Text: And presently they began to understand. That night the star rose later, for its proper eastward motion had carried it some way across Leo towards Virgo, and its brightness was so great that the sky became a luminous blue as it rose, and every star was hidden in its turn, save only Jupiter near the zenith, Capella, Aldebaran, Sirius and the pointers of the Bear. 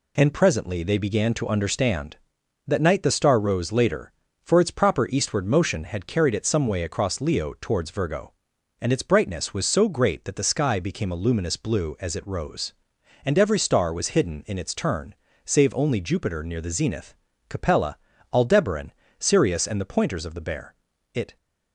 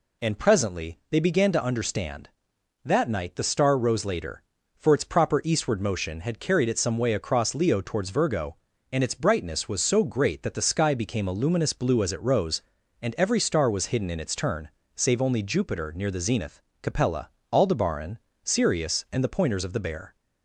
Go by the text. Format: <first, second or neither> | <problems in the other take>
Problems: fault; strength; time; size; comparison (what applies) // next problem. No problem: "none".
second | goes on to say "It"; slight; from 21.1 s on; 0.24 s long